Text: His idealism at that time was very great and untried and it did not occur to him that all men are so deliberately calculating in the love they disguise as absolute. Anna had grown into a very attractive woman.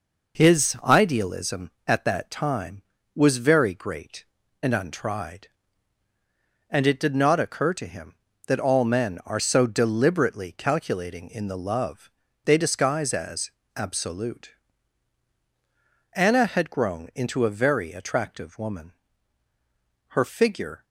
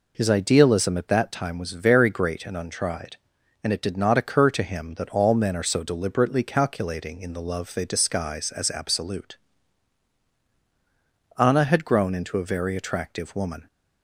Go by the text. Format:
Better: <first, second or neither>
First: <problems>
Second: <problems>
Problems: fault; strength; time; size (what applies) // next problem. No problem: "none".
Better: second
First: pauses between "love" and "they"; slight; at 12.1 s; 0.32 s long // pauses between "as" and "absolute"; slight; at 13.5 s; 0.26 s long // goes on to say "Her figure"; noticeable; from 20.0 s on; 0.76 s long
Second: none